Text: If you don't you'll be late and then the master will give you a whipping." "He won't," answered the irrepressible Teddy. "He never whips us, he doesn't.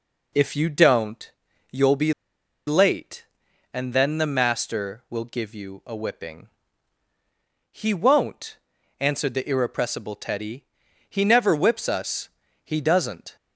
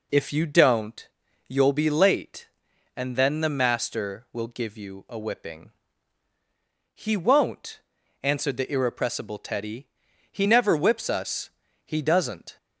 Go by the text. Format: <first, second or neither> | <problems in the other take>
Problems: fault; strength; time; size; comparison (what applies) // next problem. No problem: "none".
second | pauses between "don't" and "you'll"; at 1.2 s; 0.40 s long; also in the second // pauses between "be" and "late"; noticeable; at 2.1 s; 0.54 s long